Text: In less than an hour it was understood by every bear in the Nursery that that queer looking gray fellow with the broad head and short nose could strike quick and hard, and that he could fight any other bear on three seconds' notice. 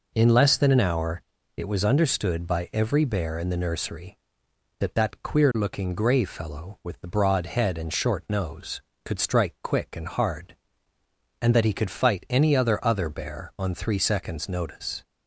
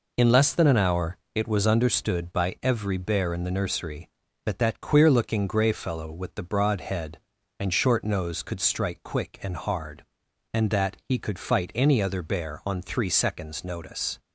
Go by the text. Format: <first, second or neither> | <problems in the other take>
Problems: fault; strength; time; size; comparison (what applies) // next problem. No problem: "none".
second | pauses between "hour" and "it"; slight; at 1.2 s; 0.34 s long; slight in the second // says "other" twice; at 12.8 s